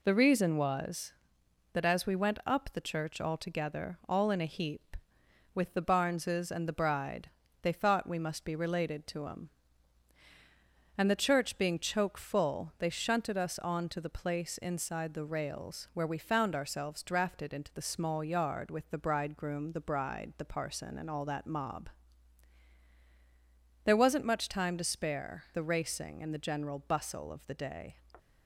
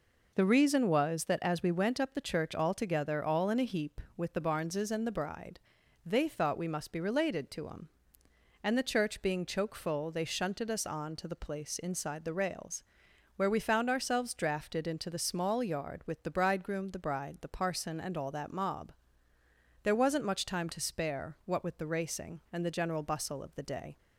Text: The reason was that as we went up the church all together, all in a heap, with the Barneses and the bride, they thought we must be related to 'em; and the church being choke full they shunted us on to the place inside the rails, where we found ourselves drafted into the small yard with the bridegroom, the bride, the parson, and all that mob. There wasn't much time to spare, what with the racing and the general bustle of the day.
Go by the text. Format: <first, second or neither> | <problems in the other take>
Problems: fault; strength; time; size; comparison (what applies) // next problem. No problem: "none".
second | skips "what with"; at 25.4 s